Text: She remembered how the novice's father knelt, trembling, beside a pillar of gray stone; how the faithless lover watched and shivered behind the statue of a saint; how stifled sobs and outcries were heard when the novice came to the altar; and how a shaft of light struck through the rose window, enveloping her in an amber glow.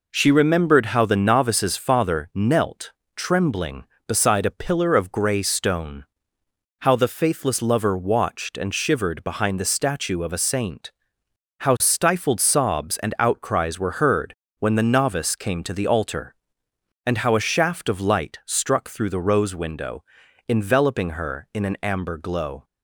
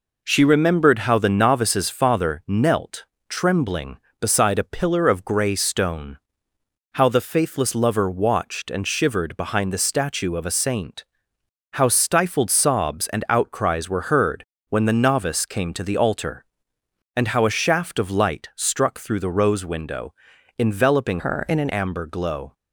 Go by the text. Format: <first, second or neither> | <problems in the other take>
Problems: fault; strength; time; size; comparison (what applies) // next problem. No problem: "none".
first | pauses between "heard" and "when"; slight; at 14.4 s; 0.24 s long; slight in the first // changes voice from "her" to "an"; from 21.1 to 21.6 s; 0.5 s long